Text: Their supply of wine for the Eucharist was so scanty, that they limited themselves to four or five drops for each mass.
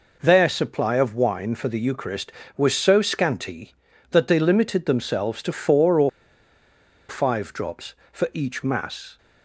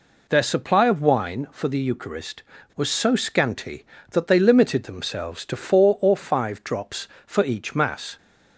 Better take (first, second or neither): second